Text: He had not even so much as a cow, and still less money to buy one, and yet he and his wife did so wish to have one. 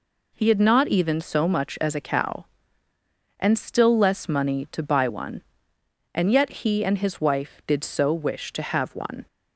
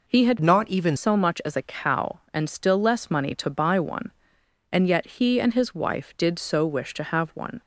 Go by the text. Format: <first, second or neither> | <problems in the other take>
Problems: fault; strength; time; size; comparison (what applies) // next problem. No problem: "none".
first | changes voice from "not" to "even"; from 0.4 to 0.9 s; 0.5 s long